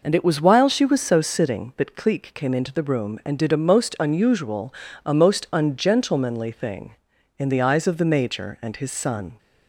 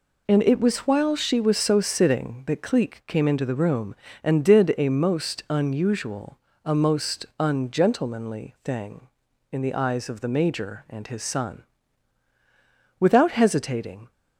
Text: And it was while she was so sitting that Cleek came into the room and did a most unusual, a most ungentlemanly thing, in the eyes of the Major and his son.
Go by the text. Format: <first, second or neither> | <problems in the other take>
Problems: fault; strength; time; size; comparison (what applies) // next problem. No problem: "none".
first | goes on to say "Without hesitating"; noticeable; from 12.9 s on; 1.1 s long